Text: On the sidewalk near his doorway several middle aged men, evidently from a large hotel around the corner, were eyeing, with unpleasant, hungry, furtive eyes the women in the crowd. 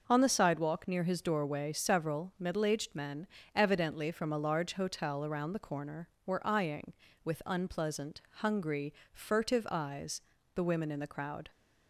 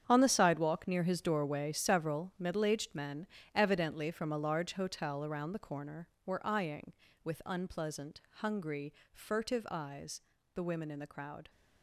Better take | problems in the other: first | gets quieter; strong; throughout; 13 dB // pauses between "eyes" and "the"; slight; at 10.2 s; 0.32 s long; slight in the first

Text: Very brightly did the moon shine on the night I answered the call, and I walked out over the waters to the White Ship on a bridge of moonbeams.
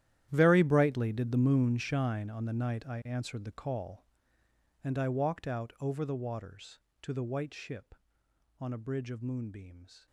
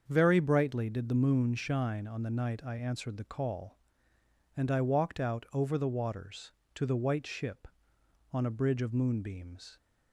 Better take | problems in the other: second | gets quieter; strong; throughout; 17.5 dB // starts louder than the rest; strong; until 1.3 s; 12 dB; also in the second

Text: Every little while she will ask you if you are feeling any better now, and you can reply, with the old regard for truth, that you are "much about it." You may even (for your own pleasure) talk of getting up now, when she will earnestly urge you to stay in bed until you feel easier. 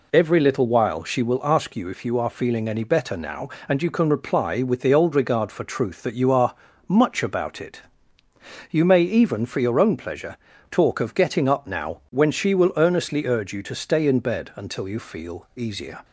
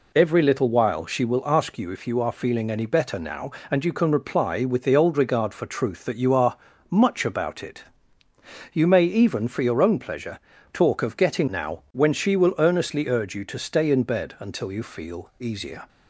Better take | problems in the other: first | pauses between "are" and "much"; slight; at 6.5 s; 0.32 s long; slight in the first // skips "up"; at 11.4 s

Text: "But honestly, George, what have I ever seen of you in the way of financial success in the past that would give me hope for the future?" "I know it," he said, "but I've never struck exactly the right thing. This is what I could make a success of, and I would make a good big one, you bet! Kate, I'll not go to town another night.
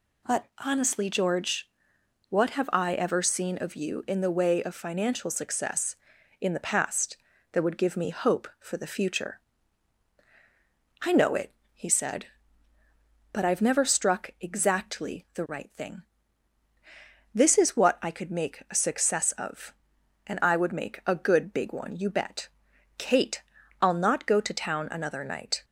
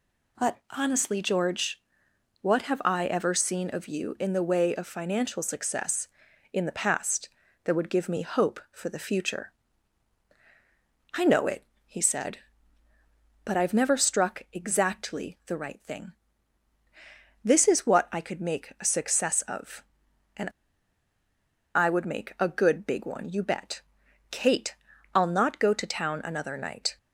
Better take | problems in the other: first | pauses between "and" and "I"; strong; at 20.4 s; 1.2 s long

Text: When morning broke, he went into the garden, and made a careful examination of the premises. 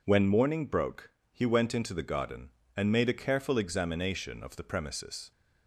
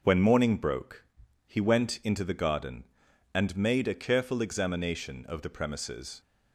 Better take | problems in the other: neither | none

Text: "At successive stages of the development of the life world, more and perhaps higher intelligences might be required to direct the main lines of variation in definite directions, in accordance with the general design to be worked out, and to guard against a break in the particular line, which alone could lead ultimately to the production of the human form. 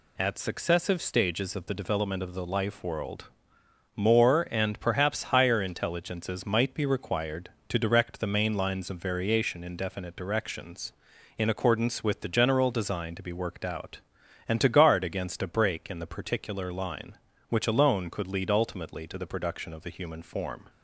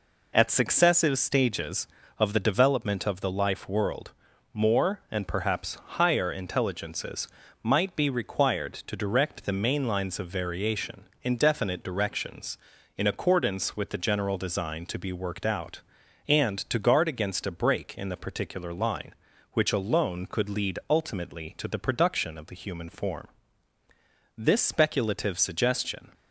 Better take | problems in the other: first | pauses between "intelligences" and "might"; slight; at 7.2 s; 0.34 s long // goes on to say "This speculative suggestion"; strong; from 24.3 s on; 1.7 s long

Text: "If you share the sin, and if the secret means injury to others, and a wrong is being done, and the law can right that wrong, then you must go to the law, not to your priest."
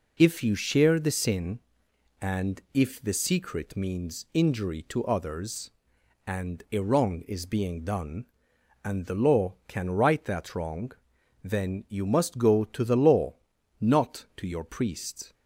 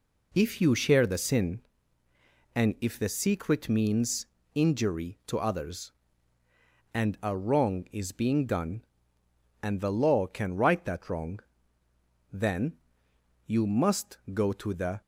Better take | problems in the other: first | pauses between "means" and "injury"; slight; at 4.2 s; 0.28 s long // pauses between "then" and "you"; noticeable; at 12.7 s; 0.70 s long // stops before "law not to your priest"; at 15.0 s

